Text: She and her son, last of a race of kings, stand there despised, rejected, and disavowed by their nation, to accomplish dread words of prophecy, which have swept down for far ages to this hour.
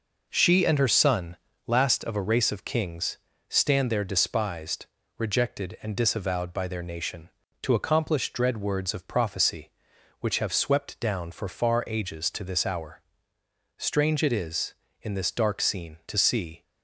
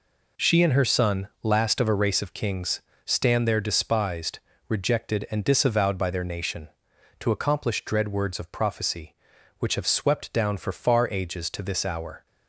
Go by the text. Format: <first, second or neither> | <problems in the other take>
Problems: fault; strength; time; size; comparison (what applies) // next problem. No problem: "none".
second | goes on to say "Strange it is in this dark scene to see"; strong; from 13.7 s on; 2.8 s long